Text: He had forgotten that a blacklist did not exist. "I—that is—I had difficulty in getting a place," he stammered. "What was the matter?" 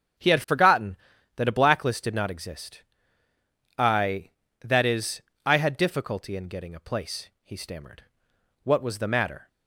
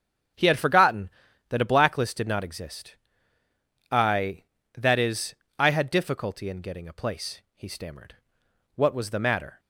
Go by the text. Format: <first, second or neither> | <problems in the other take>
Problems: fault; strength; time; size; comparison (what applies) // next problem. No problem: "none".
neither | starts louder than the rest; strong; the same in both